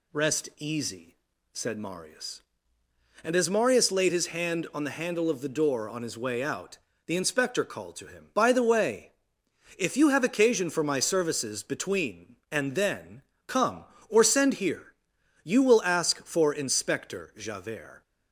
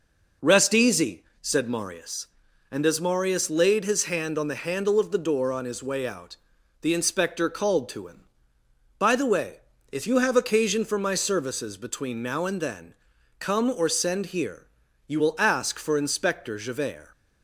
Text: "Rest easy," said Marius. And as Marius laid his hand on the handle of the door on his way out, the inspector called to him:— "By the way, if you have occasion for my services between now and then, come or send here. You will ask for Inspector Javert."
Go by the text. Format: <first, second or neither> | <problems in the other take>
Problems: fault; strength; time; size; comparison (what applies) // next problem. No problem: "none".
second | skips "now"; at 12.4 s